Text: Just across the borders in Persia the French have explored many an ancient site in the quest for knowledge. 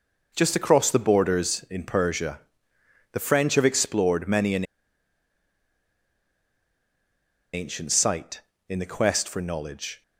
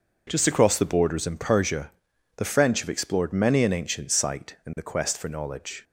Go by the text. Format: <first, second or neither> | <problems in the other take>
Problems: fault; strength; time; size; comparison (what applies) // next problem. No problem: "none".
second | pauses between "Persia" and "the"; noticeable; at 2.4 s; 0.72 s long; noticeable in the second // pauses between "an" and "ancient"; strong; at 4.6 s; 2.8 s long